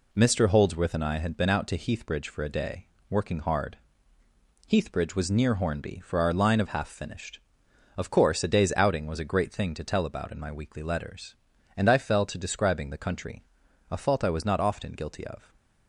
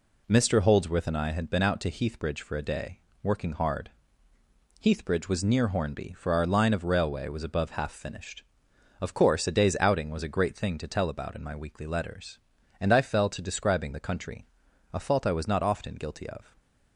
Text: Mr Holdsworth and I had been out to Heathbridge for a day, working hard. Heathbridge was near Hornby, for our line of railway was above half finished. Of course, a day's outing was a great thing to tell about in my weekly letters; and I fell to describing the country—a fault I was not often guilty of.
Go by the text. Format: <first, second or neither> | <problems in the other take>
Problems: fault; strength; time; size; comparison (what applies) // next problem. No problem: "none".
second | skips "railway was above"; at 6.6 s